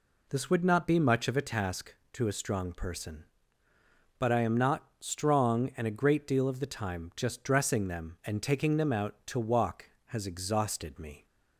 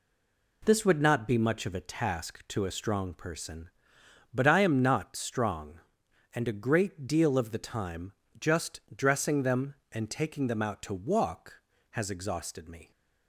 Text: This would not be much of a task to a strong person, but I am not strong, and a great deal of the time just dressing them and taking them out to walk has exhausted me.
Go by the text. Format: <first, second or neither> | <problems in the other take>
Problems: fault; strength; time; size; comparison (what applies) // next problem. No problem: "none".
first | stays silent before the first word; slight; until 0.6 s; 0.6 s long // pauses between "time" and "just"; slight; at 8.1 s; 0.26 s long